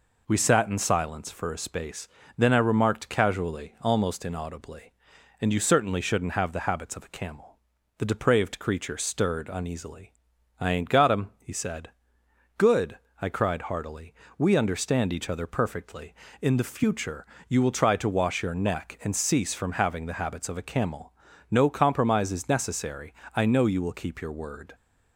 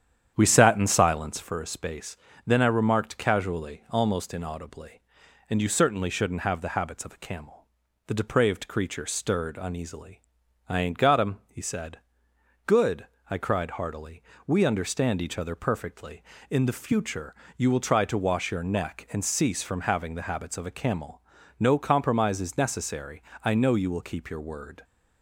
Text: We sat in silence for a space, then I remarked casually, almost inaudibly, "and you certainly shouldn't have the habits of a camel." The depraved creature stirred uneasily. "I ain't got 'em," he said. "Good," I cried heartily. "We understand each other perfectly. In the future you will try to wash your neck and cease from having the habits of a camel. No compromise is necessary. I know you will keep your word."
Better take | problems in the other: first | starts louder than the rest; strong; until 1.5 s; 9 dB // pauses between "future" and "you"; slight; at 17.3 s; 0.20 s long; slight in the first

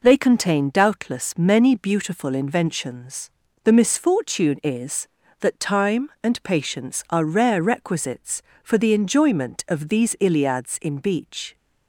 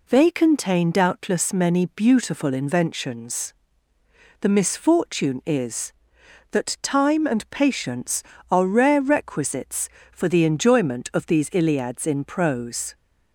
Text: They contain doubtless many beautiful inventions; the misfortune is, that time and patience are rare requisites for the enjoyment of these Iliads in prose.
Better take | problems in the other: second | says "beach" for "prose"; at 10.9 s

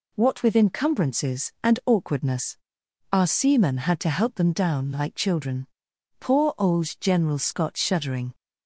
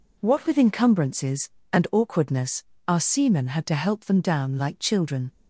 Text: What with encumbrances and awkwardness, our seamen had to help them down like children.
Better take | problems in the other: second | goes on to say "Poor old General Scott shuddering"; strong; from 6.1 s on; 2.1 s long

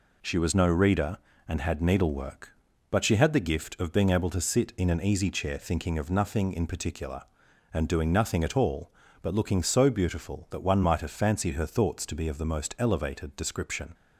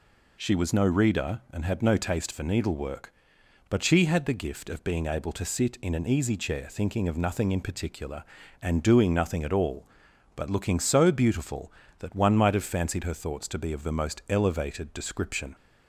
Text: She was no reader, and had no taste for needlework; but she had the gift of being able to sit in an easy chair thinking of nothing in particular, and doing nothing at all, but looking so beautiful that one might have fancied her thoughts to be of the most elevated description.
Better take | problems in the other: second | skips "no taste for"; at 1.8 s

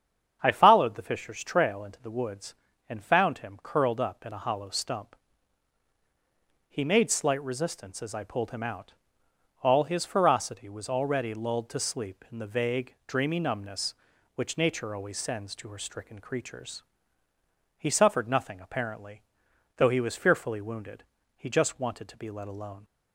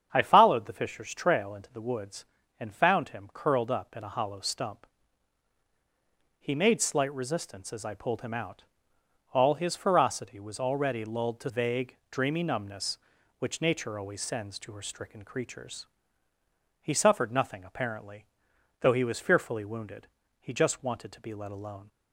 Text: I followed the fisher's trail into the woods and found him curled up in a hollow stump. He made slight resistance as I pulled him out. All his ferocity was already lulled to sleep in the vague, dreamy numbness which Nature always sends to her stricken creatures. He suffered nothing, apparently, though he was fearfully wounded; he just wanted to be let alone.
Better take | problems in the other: first | starts louder than the rest; strong; until 1.1 s; 8 dB; strong in the first // skips "sleep in the"; at 11.4 s

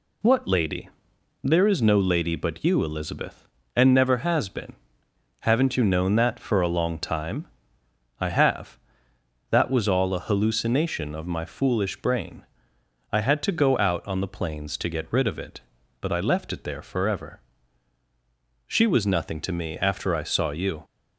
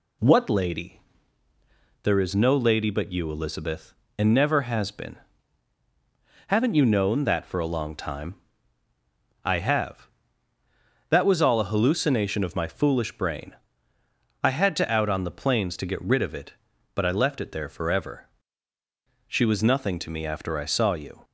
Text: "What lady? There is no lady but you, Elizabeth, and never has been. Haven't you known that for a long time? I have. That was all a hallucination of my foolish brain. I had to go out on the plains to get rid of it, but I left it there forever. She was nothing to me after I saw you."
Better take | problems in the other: first | skips "go"; at 14.9 s

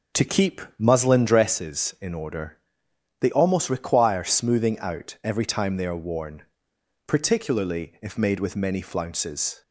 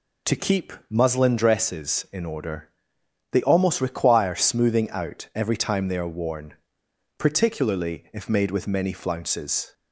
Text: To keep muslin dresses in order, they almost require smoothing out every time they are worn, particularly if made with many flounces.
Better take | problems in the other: second | starts louder than the rest; until 1.6 s; 7 dB // pauses between "keep" and "muslin"; slight; at 0.5 s; 0.18 s long; slight in the second

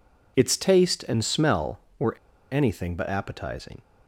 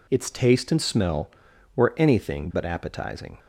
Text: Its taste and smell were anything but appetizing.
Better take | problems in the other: second | pauses between "were" and "anything"; at 2.1 s; 0.37 s long

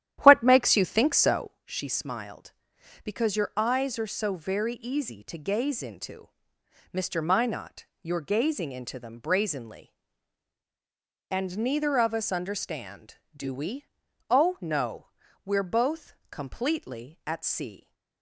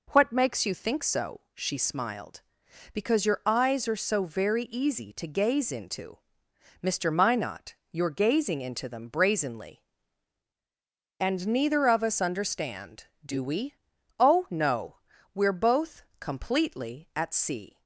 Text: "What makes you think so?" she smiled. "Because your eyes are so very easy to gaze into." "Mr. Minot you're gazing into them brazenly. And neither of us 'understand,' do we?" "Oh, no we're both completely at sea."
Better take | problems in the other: second | starts louder than the rest; strong; until 1.6 s; 11.5 dB // pauses between "Minot" and "you're"; slight; at 7.8 s; 0.16 s long; slight in the second // pauses between "no" and "we're"; at 15.0 s; 0.40 s long; also in the second

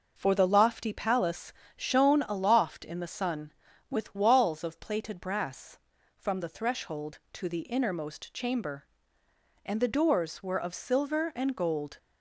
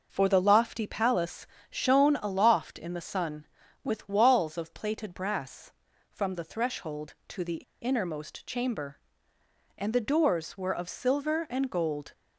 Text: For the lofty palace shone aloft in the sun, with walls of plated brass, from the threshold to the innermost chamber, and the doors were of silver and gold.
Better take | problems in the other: first | starts louder than the rest; noticeable; until 1.1 s; 6 dB // pauses between "palace" and "shone"; slight; at 1.4 s; 0.22 s long; slight in the first // pauses between "the" and "innermost"; slight; at 7.6 s; 0.18 s long

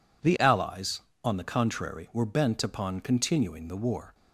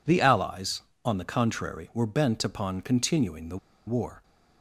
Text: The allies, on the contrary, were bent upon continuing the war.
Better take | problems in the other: first | pauses between "the" and "war"; slight; at 3.5 s; 0.29 s long

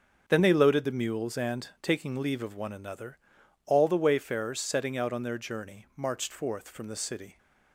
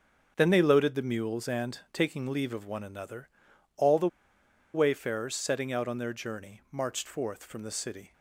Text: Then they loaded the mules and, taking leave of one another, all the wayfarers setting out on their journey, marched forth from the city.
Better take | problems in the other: first | starts louder than the rest; until 1.3 s; 6.5 dB; also in the first // pauses between "the" and "wayfarers"; noticeable; at 4.0 s; 0.65 s long

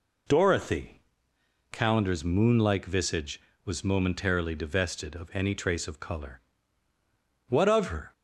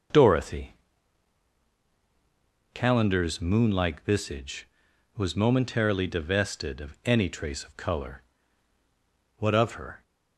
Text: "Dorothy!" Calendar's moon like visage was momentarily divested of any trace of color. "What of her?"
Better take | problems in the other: neither | none

